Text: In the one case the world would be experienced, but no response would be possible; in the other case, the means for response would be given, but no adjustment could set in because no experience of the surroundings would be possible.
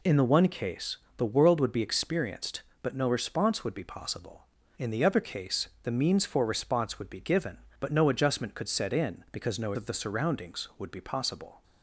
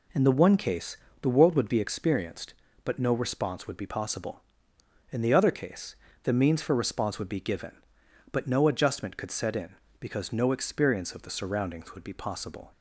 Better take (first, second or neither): second